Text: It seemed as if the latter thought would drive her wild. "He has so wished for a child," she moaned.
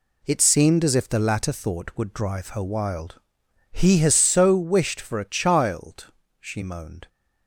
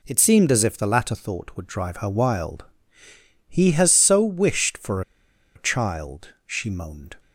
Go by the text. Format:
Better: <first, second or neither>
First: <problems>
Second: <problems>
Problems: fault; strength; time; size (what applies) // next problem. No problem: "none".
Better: first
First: none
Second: pauses between "for" and "a"; noticeable; at 5.0 s; 0.54 s long